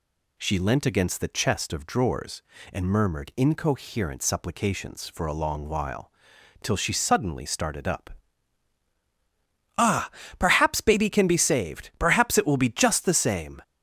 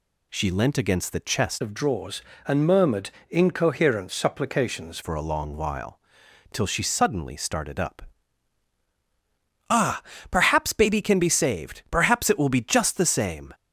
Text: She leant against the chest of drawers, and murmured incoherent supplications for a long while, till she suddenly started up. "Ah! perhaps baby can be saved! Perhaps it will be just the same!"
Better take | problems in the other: first | changes voice from "of" to "supplications"; from 1.6 to 4.9 s; 3.3 s long // pauses between "murmured" and "incoherent"; slight; at 3.0 s; 0.20 s long

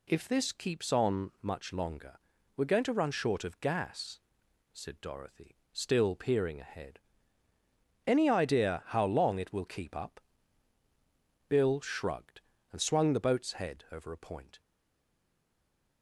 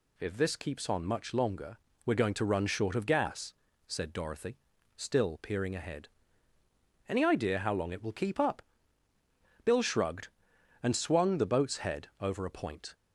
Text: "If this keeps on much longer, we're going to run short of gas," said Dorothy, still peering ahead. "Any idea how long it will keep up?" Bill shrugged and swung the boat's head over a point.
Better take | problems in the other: second | stays silent after the last word; noticeable; from 14.6 s on; 1.4 s long

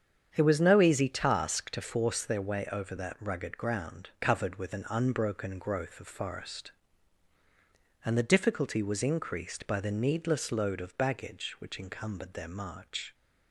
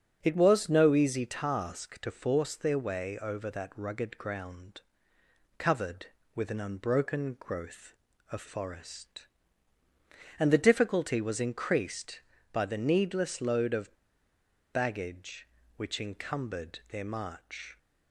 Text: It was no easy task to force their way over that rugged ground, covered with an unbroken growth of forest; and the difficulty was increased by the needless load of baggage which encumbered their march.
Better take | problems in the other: first | starts louder than the rest; until 1.2 s; 7 dB; strong in the first // pauses between "of" and "baggage"; noticeable; at 13.9 s; 0.78 s long

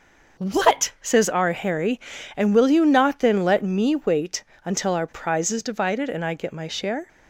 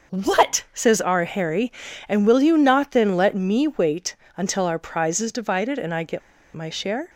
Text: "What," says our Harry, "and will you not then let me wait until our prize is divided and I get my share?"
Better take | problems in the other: first | starts louder than the rest; noticeable; until 1.2 s; 6 dB; noticeable in the first // pauses between "wait" and "until"; slight; at 4.1 s; 0.20 s long; slight in the first // pauses between "get" and "my"; slight; at 6.2 s; 0.35 s long

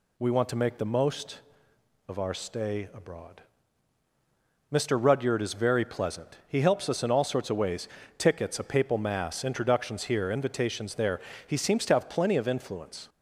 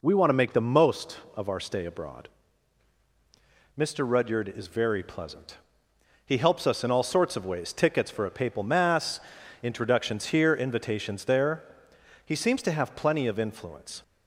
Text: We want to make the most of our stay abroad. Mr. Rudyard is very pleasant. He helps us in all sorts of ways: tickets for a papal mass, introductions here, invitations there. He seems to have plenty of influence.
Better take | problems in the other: second | skips "for"; at 8.5 s

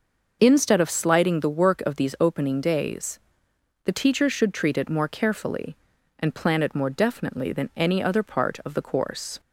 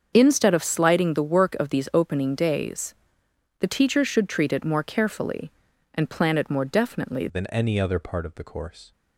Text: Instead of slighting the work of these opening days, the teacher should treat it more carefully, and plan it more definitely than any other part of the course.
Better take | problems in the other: first | starts louder than the rest; until 1.1 s; 7 dB // changes voice at "than"; from 7.2 s on; 1.7 s long

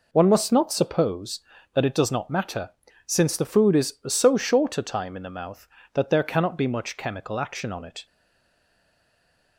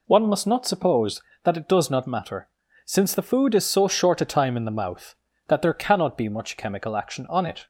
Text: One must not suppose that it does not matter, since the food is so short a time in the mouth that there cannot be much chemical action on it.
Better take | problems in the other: second | stays silent after the last word; noticeable; from 8.0 s on; 1.5 s long

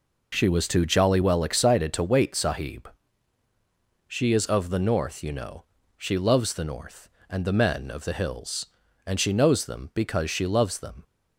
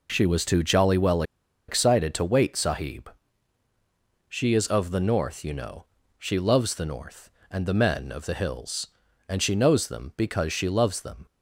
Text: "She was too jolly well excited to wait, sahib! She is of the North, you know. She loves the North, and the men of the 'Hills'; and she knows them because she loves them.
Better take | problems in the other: first | pauses between "well" and "excited"; at 1.2 s; 0.45 s long

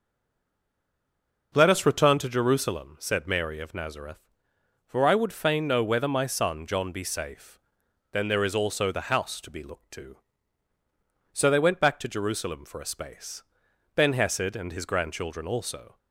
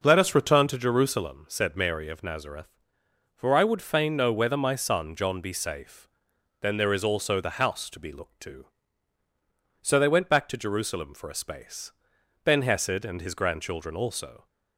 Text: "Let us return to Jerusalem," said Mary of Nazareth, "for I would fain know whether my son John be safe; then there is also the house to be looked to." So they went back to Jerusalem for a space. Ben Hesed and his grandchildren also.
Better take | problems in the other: second | stays silent before the first word; noticeable; until 1.5 s; 1.5 s long

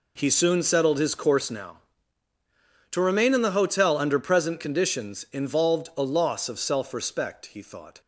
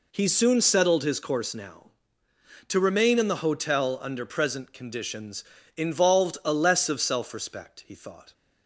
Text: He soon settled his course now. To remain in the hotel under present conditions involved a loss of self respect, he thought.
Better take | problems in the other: first | pauses between "conditions" and "involved"; slight; at 5.4 s; 0.34 s long // says "less" for "loss"; at 6.5 s

